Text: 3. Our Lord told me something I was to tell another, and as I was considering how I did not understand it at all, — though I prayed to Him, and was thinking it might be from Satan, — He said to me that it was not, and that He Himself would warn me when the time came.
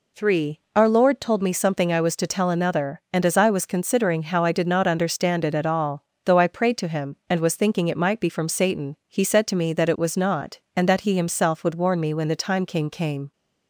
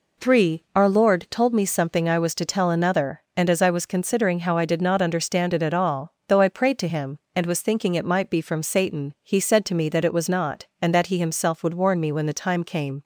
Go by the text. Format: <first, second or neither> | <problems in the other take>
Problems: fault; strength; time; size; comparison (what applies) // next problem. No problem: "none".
second | says "came" twice; at 12.8 s